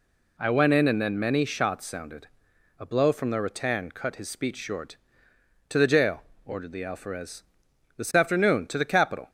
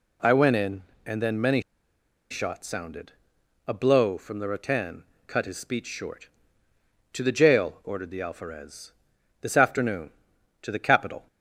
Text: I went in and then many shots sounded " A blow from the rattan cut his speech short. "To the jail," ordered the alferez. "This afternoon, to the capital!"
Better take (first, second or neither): first